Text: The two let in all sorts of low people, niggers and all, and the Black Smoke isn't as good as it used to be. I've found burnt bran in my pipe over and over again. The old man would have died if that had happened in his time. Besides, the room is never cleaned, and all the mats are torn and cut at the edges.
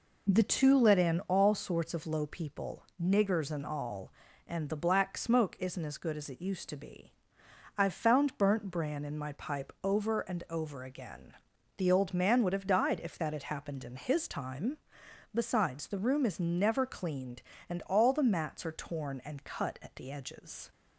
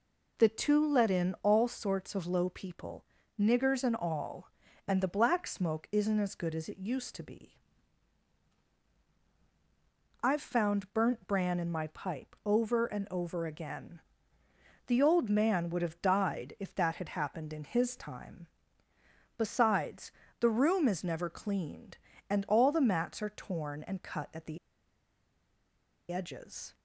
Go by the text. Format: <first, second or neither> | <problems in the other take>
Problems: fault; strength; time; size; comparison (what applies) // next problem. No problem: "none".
first | pauses between "the" and "edges"; strong; at 24.5 s; 1.5 s long